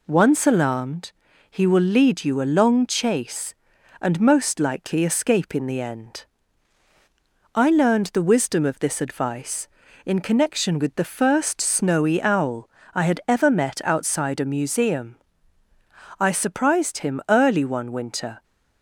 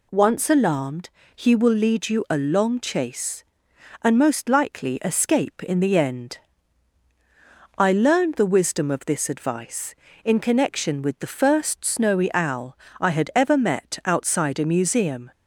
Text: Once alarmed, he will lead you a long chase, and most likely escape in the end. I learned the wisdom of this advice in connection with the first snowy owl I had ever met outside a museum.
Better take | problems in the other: second | pauses between "owl" and "I"; slight; at 12.6 s; 0.24 s long; slight in the second // goes on to say "I surprised him early one winter"; strong; from 16.1 s on; 2.2 s long

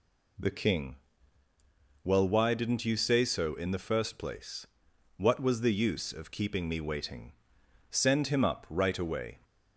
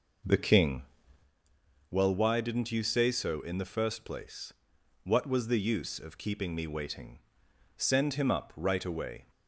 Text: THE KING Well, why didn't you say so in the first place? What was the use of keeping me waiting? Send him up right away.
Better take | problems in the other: first | starts louder than the rest; noticeable; until 1.3 s; 5.5 dB // pauses between "KING" and "Well"; at 0.8 s; 1.0 s long; also in the first

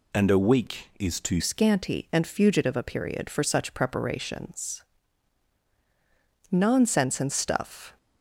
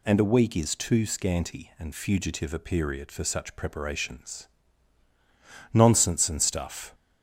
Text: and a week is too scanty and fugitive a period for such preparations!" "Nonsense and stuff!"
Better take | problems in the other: second | changes voice at "scanty"; from 1.3 s on; 6.6 s long

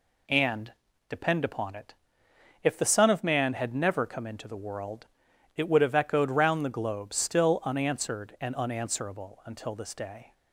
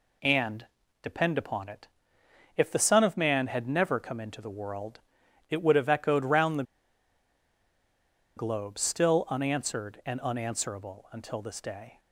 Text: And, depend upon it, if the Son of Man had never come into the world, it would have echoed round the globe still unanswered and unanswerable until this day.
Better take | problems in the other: first | pauses between "the" and "globe"; strong; at 6.6 s; 1.7 s long

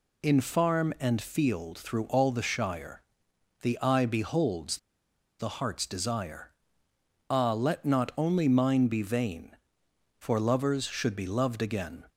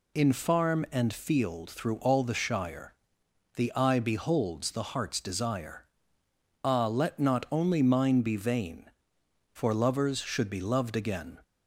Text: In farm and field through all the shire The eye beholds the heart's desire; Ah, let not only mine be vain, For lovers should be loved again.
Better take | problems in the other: second | pauses between "shire" and "The"; noticeable; at 3.0 s; 0.58 s long; noticeable in the second // pauses between "beholds" and "the"; noticeable; at 4.7 s; 0.61 s long

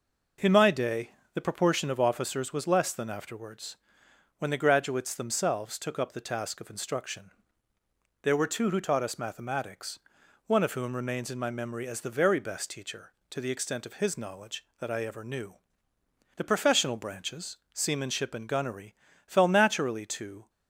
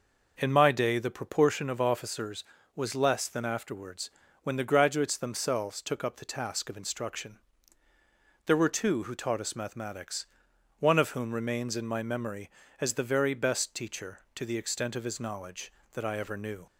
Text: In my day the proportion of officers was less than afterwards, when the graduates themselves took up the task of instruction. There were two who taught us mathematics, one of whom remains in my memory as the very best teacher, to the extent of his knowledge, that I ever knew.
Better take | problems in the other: second | pauses between "day" and "the"; slight; at 1.0 s; 0.24 s long // goes on to say "The professional branches seamanship and gunnery fell naturally to"; strong; from 16.3 s on; 4.1 s long

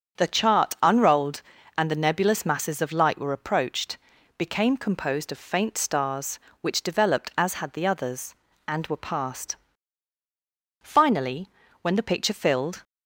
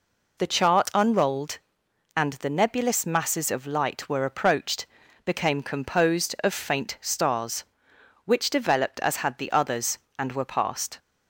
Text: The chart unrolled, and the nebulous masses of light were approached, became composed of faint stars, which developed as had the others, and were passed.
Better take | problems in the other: second | starts louder than the rest; strong; until 1.2 s; 7.5 dB // goes on to say "Finally when the picture filled"; strong; from 10.8 s on; 2.0 s long

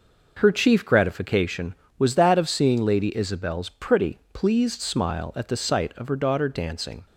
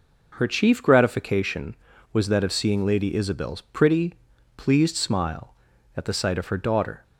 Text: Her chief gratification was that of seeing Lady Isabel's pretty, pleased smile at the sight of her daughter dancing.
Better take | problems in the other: first | stops before "dancing"; at 7.0 s

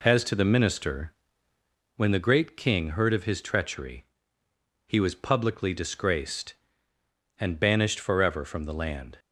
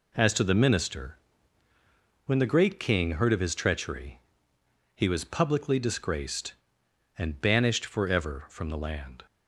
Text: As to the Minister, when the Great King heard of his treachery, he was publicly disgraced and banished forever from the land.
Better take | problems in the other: neither | none

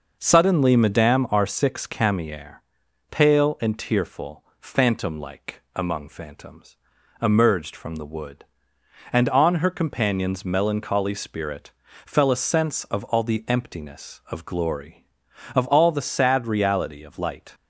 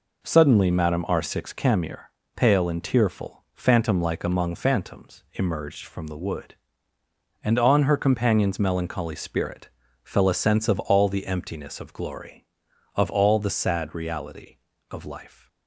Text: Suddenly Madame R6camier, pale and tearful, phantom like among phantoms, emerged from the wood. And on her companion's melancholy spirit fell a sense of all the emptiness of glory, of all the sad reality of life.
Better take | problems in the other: second | pauses between "like" and "among"; slight; at 5.6 s; 0.16 s long // pauses between "spirit" and "fell"; slight; at 11.7 s; 0.34 s long; slight in the second // says "light" for "life"; at 17.1 s

